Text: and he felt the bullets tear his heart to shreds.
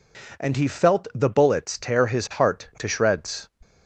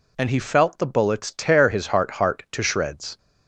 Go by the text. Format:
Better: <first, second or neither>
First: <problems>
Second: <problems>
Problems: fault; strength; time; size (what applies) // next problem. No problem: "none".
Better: first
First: none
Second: says "heart" twice; at 2.1 s